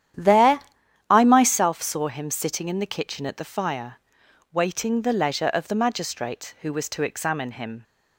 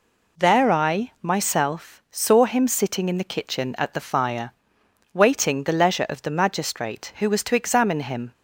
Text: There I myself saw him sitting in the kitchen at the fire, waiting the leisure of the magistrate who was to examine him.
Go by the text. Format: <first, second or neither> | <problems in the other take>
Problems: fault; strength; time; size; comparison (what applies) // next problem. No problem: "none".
second | starts louder than the rest; strong; until 1.7 s; 10.5 dB // pauses between "There" and "I"; noticeable; at 0.5 s; 0.50 s long